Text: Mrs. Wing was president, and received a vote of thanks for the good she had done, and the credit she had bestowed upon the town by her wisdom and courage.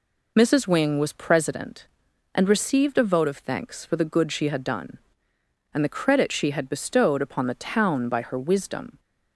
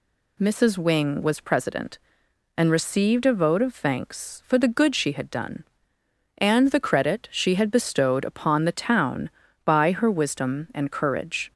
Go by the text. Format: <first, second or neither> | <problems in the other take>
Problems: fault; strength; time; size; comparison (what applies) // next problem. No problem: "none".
second | stops before "and courage"; at 8.9 s